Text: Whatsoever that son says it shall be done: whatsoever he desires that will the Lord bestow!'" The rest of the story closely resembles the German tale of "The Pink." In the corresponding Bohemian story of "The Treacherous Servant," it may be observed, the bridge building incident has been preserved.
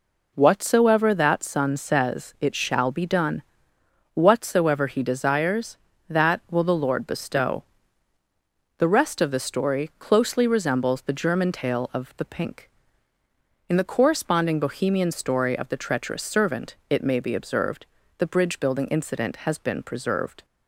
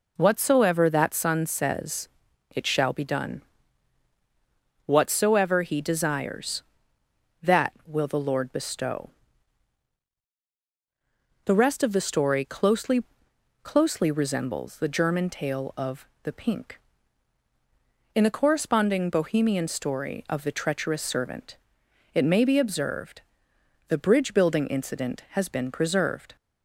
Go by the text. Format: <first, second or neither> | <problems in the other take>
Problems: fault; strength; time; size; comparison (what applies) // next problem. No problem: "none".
first | pauses between "says" and "it"; noticeable; at 2.0 s; 0.46 s long // says "closely" twice; at 13.6 s // pauses between "of" and "The"; slight; at 16.0 s; 0.16 s long